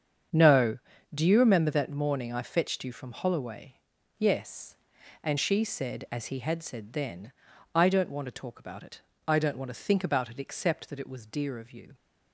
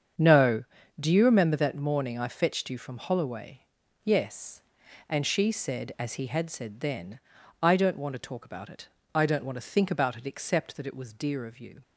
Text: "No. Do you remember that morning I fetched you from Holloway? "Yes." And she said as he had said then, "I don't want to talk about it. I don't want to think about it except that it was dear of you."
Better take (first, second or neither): neither